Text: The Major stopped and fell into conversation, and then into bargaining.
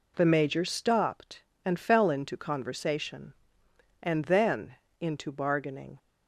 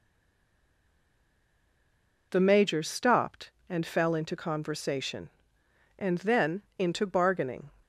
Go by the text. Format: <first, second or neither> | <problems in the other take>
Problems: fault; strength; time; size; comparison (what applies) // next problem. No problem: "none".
first | stays silent before the first word; until 2.3 s; 2.3 s long // pauses between "then" and "into"; slight; at 6.6 s; 0.16 s long; slight in the first